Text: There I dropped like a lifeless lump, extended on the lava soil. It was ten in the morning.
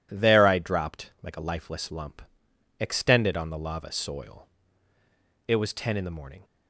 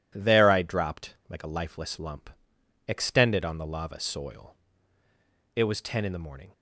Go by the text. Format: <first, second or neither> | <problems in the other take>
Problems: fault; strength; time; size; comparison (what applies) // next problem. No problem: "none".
neither | none